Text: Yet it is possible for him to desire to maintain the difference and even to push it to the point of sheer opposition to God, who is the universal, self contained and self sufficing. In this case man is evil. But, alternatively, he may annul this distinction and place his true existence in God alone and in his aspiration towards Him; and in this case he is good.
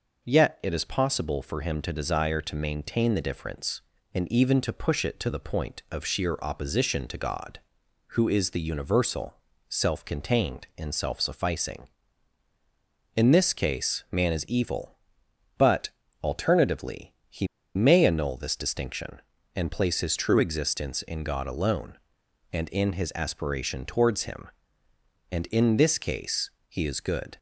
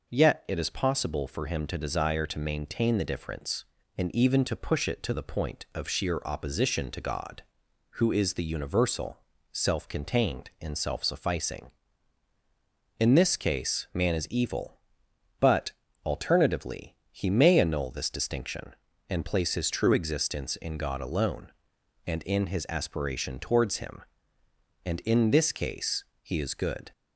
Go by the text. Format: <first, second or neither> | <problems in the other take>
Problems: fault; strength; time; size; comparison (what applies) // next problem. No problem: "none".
second | pauses between "he" and "may"; slight; at 17.4 s; 0.28 s long // pauses between "case" and "he"; slight; at 26.4 s; 0.18 s long; slight in the second